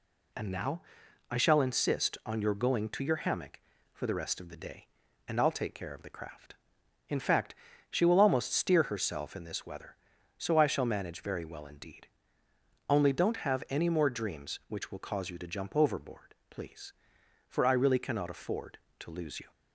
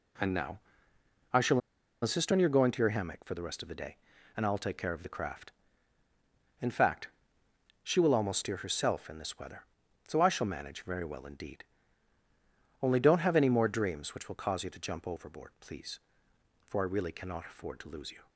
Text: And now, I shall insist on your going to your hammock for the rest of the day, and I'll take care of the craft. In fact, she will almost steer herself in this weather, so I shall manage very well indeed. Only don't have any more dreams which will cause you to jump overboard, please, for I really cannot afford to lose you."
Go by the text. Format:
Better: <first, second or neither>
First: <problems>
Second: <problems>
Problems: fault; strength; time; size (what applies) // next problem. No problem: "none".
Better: first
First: none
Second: pauses between "shall" and "insist"; at 1.5 s; 0.43 s long